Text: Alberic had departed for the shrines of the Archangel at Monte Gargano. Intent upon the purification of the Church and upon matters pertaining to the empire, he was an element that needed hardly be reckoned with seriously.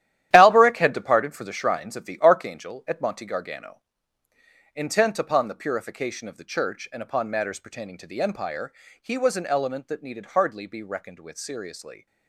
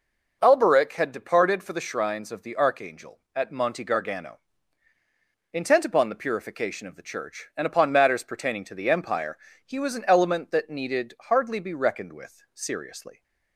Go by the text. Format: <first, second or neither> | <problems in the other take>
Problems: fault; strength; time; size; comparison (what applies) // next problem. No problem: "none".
second | gets quieter; strong; throughout; 10 dB